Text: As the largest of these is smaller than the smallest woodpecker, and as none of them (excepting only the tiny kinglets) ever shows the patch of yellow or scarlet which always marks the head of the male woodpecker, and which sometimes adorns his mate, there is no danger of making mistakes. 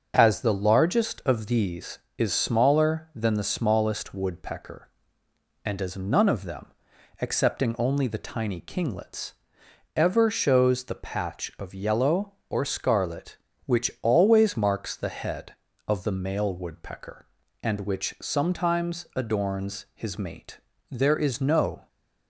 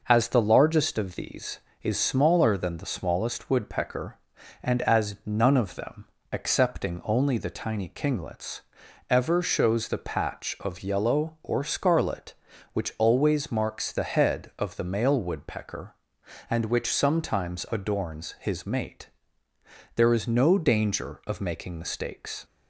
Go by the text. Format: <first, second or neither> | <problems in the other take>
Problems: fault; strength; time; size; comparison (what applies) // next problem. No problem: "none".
second | starts louder than the rest; until 1.1 s; 6.5 dB // stops before "danger of making mistakes"; at 21.8 s